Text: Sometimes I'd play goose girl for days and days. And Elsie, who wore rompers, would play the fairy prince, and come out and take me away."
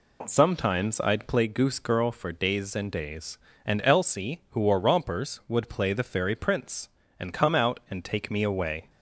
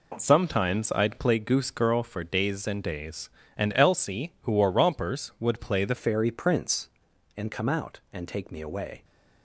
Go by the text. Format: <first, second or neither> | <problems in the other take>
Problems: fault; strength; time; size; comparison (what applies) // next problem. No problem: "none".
first | changes voice at "fairy"; from 5.9 s on; 3.1 s long